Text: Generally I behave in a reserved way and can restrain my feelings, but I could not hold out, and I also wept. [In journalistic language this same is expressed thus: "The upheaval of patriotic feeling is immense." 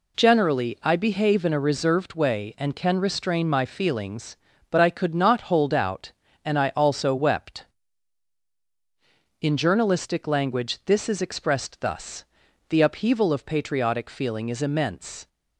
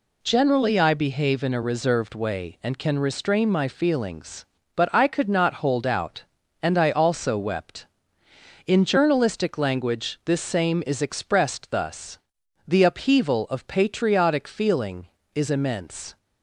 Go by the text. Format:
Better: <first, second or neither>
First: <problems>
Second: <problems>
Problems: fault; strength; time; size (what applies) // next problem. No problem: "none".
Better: second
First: skips "same"; at 11.0 s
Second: none